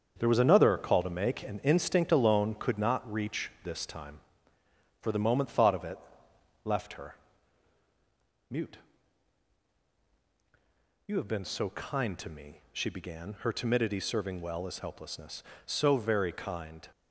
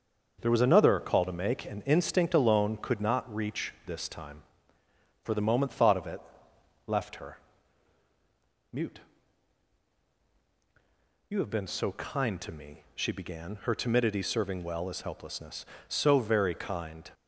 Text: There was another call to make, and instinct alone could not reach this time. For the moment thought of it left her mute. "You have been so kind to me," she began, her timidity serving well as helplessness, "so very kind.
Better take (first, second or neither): second